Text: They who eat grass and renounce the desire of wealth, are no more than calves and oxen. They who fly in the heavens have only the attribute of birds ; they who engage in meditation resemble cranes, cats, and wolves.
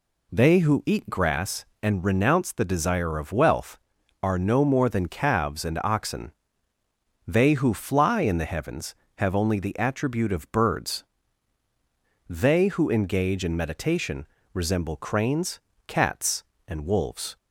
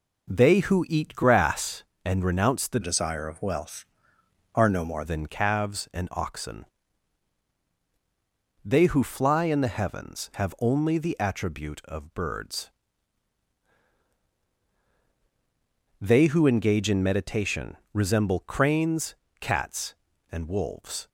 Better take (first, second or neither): first